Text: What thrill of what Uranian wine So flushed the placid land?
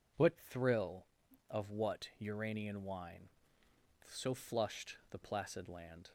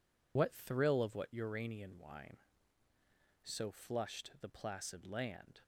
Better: first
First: none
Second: loses the start of "What"; at 0.3 s; 55 ms

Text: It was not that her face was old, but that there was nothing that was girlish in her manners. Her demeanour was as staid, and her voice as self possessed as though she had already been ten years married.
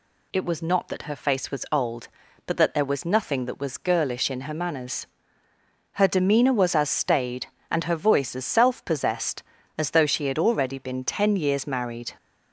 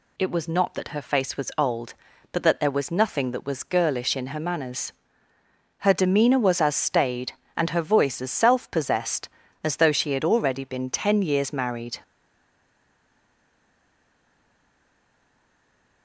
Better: first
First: none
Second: stays silent after the last word; strong; from 12.0 s on; 4.0 s long

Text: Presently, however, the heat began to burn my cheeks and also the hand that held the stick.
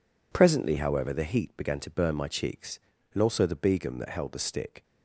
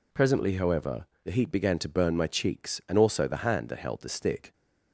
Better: second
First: says "begum" for "hand"; at 3.5 s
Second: none

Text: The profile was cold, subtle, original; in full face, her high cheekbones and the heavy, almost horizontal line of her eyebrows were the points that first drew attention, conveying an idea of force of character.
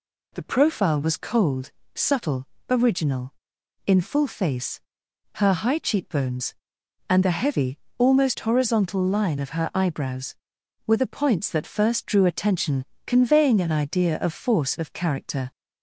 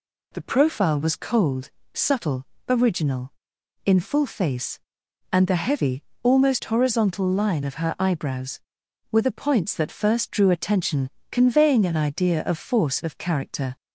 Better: first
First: none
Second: skips "her high cheekbones"; at 5.0 s

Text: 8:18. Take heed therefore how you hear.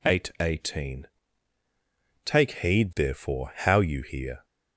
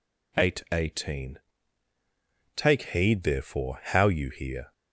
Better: neither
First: none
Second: none

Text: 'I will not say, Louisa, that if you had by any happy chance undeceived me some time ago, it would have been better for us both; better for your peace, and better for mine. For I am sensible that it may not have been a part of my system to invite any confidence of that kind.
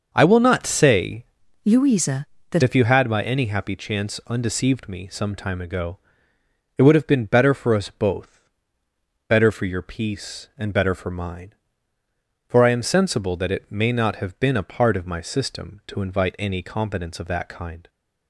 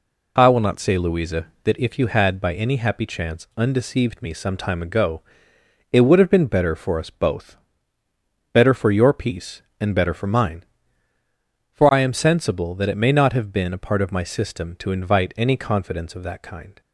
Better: second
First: starts louder than the rest; noticeable; until 1.1 s; 6 dB // changes voice from "Louisa" to "that"; from 1.6 to 2.6 s; 1.0 s long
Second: none

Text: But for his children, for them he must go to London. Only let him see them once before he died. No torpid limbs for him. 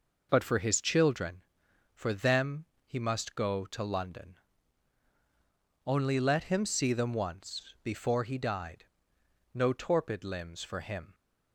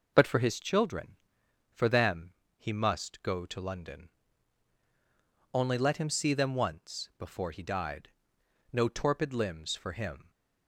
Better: neither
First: pauses between "them" and "he"; slight; at 2.6 s; 0.22 s long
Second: pauses between "them" and "he"; slight; at 2.3 s; 0.22 s long

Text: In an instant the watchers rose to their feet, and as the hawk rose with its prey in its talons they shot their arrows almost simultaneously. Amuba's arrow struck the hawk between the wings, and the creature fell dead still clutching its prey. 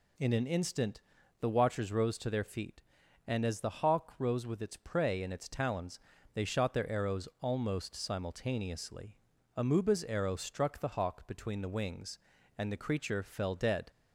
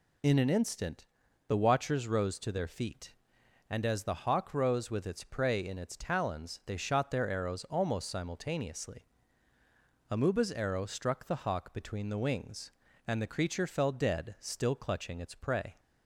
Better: second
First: pauses between "instant" and "the"; at 0.9 s; 0.40 s long // pauses between "talons" and "they"; slight; at 5.9 s; 0.36 s long // stops before "still clutching its prey"; at 13.8 s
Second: pauses between "instant" and "the"; at 1.0 s; 0.42 s long

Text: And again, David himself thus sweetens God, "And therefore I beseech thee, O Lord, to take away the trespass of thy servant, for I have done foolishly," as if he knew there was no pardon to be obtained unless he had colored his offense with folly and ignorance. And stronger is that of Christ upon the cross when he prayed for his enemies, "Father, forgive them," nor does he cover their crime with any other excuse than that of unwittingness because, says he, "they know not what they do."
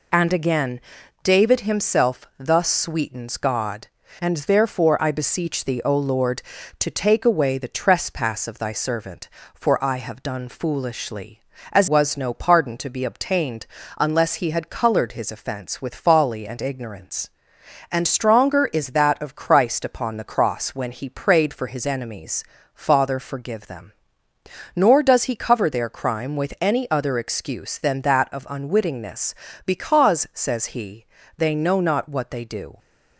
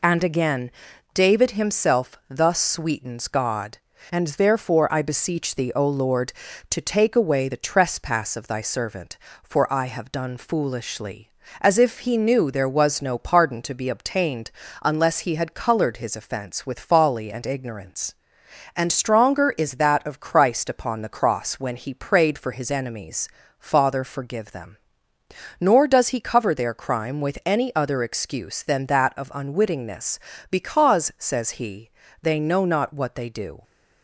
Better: second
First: skips "if he knew there"; at 11.8 s // pauses between "obtained" and "unless"; slight; at 13.6 s; 0.32 s long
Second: pauses between "obtained" and "unless"; slight; at 14.5 s; 0.32 s long

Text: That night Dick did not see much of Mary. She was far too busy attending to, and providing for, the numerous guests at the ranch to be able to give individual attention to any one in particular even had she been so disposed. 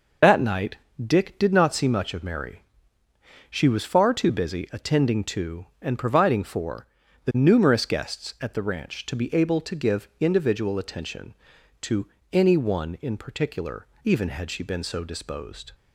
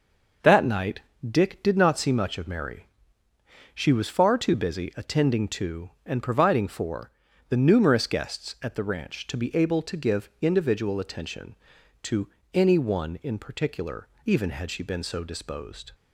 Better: second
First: loses the start of "That"; at 0.2 s; 50 ms // pauses between "night" and "Dick"; slight; at 0.7 s; 0.26 s long // pauses between "to" and "any"; slight; at 12.0 s; 0.26 s long // pauses between "particular" and "even"; slight; at 13.8 s; 0.16 s long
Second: pauses between "night" and "Dick"; slight; at 1.0 s; 0.26 s long // pauses between "to" and "any"; slight; at 12.2 s; 0.26 s long // pauses between "particular" and "even"; slight; at 14.0 s; 0.16 s long

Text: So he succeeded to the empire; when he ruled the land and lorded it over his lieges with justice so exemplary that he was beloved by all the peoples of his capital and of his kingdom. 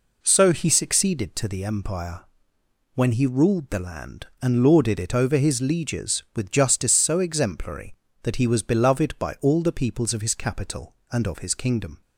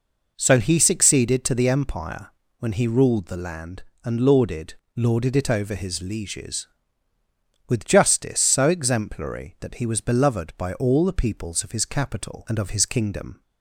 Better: first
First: none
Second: says "lorded" twice; at 4.9 s

